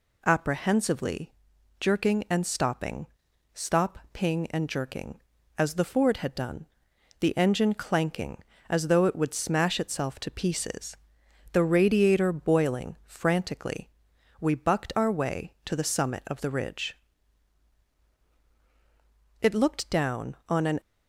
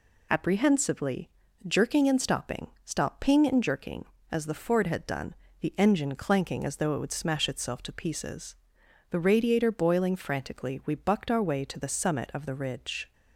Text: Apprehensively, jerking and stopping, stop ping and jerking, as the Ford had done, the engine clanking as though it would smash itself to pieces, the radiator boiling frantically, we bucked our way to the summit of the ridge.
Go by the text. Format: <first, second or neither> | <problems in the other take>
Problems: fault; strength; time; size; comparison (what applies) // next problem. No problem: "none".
second | goes on to say "It looked down on an"; from 19.4 s on; 1.3 s long